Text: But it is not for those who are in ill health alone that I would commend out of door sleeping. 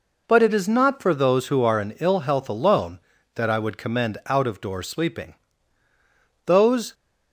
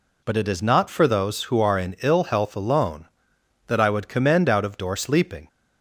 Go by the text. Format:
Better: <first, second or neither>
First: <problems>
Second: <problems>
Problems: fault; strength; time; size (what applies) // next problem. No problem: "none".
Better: second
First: goes on to say "Those"; slight; from 6.4 s on; 0.48 s long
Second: none